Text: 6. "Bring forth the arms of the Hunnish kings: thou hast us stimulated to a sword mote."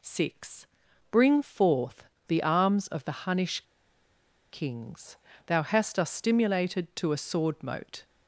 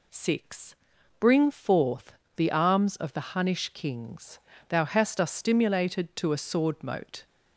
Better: second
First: pauses between "forth" and "the"; slight; at 2.0 s; 0.22 s long // pauses between "Hunnish" and "kings"; noticeable; at 3.6 s; 0.91 s long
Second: pauses between "forth" and "the"; slight; at 2.1 s; 0.22 s long

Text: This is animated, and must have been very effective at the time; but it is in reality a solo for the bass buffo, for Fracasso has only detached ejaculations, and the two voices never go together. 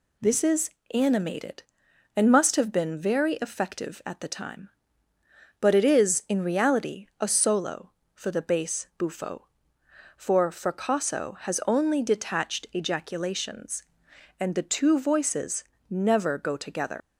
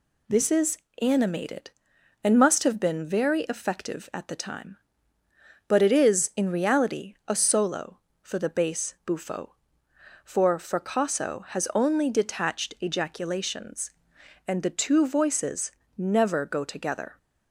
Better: second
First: pauses between "is" and "animated"; slight; at 0.6 s; 0.24 s long // pauses between "voices" and "never"; slight; at 15.6 s; 0.24 s long // leaves "together" unfinished; at 17.0 s; 95 ms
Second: pauses between "is" and "animated"; slight; at 0.7 s; 0.24 s long // pauses between "voices" and "never"; slight; at 15.7 s; 0.24 s long

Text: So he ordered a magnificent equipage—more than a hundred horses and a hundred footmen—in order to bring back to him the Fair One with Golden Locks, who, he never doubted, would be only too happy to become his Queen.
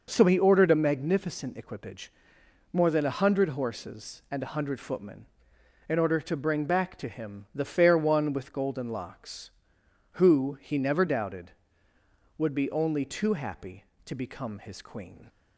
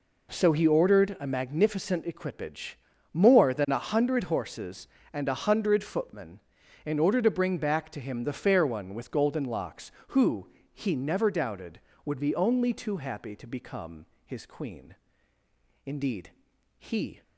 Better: first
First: none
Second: pauses between "become" and "his"; slight; at 14.0 s; 0.20 s long // goes on to say "Indeed he"; from 15.8 s on; 1.3 s long

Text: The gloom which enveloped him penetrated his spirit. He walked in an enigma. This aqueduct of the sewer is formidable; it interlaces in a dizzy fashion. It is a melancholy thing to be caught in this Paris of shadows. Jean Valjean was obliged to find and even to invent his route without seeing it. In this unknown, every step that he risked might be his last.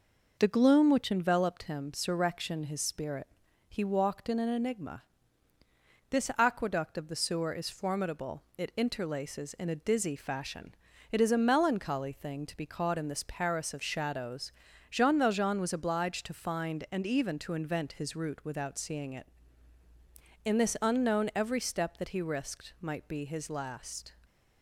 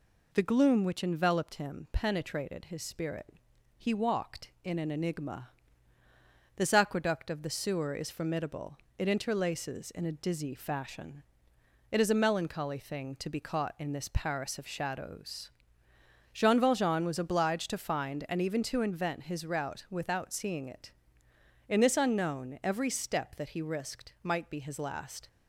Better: second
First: says "surrection" for "penetrated"; at 1.9 s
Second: none

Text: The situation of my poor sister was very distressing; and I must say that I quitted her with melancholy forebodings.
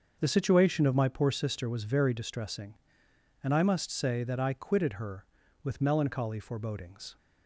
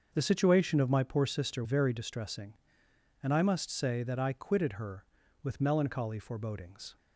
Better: first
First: starts louder than the rest; until 1.2 s; 6.5 dB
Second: starts louder than the rest; until 1.1 s; 6.5 dB // skips "was"; at 1.6 s

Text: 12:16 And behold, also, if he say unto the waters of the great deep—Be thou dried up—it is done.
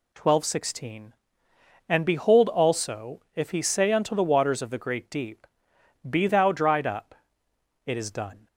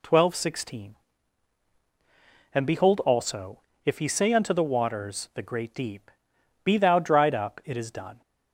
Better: first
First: none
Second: skips "of"; at 5.3 s

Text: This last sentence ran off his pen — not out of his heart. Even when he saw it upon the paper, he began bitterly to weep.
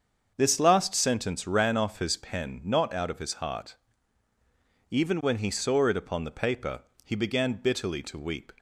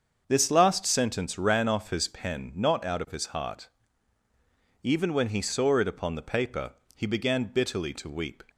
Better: neither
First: starts louder than the rest; until 1.3 s; 7 dB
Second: starts louder than the rest; until 1.2 s; 7 dB

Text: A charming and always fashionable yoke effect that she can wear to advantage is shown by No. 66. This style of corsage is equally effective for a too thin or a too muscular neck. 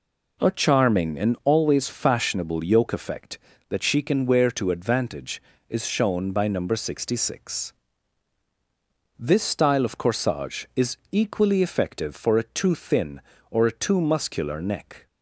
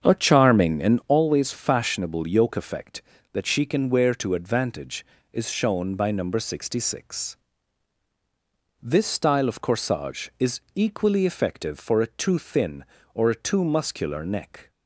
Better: first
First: pauses between "is" and "equally"; slight; at 10.9 s; 0.16 s long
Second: starts louder than the rest; strong; until 1.2 s; 7.5 dB // pauses between "is" and "equally"; slight; at 10.6 s; 0.16 s long

